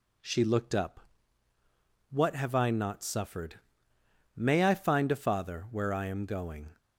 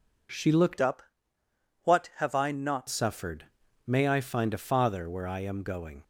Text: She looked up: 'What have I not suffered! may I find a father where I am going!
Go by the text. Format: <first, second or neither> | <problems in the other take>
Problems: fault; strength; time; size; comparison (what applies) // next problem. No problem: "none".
first | changes voice from "up" to "not"; from 0.8 to 2.8 s; 2.0 s long